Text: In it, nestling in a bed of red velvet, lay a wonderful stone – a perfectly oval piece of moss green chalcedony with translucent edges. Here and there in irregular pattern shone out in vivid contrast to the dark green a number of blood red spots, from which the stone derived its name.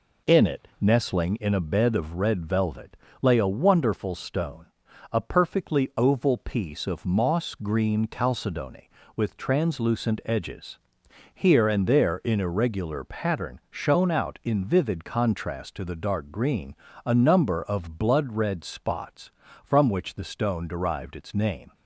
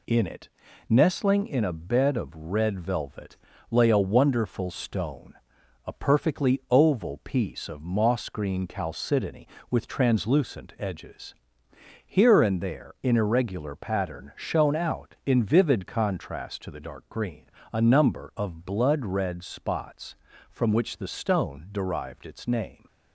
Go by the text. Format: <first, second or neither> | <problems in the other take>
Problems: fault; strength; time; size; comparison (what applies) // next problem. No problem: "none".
neither | pauses between "green" and "a"; slight; the same in both